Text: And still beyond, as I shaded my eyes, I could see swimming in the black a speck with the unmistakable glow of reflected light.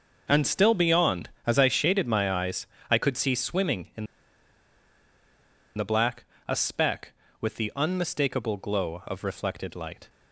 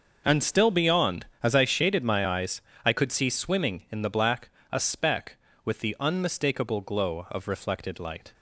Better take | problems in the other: second | pauses between "in" and "the"; strong; at 4.0 s; 1.7 s long // pauses between "black" and "a"; slight; at 6.2 s; 0.22 s long; slight in the second

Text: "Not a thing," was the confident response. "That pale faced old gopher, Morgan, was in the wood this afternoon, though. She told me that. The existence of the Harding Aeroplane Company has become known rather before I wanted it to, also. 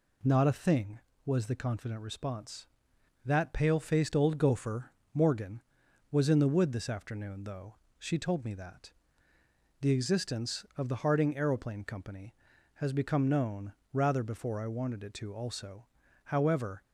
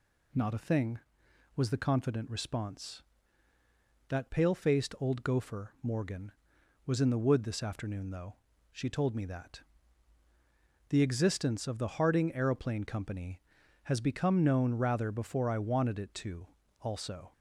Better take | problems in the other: second | pauses between "known" and "rather"; slight; at 13.7 s; 0.18 s long // goes on to say "However"; from 16.2 s on; 0.58 s long

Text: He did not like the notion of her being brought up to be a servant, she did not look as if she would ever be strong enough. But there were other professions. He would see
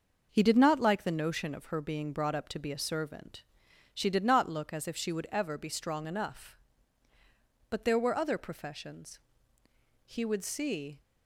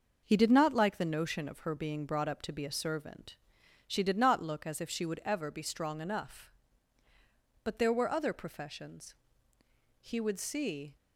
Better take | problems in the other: neither | none

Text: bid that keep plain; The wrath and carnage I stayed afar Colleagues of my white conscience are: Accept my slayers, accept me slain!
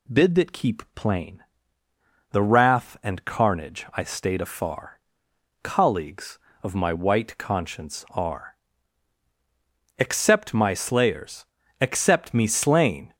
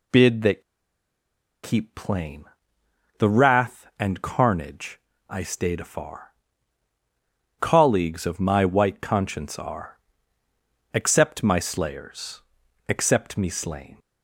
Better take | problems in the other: first | pauses between "that" and "keep"; at 0.6 s; 1.0 s long // pauses between "carnage" and "I"; slight; at 4.9 s; 0.30 s long // pauses between "afar" and "Colleagues"; strong; at 6.3 s; 1.2 s long; noticeable in the first

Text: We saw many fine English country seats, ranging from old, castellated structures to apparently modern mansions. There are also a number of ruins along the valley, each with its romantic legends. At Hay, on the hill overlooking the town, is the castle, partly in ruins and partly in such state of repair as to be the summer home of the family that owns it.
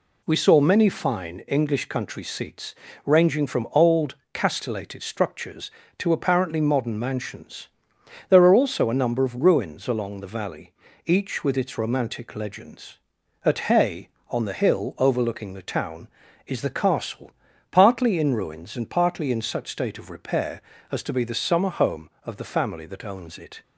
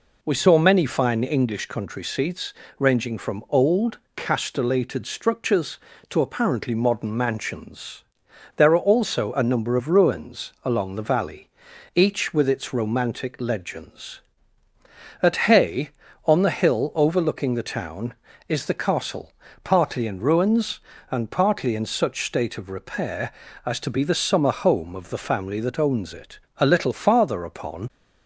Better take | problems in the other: first | goes on to say "A little farther upon"; from 26.5 s on; 1.3 s long

